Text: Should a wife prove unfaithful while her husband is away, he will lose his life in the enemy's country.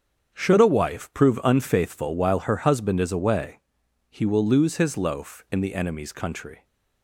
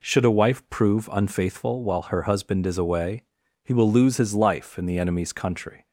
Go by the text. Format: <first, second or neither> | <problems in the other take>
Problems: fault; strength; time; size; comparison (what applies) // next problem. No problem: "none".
second | starts louder than the rest; strong; until 1.3 s; 7.5 dB // says "loaf" for "life"; at 4.9 s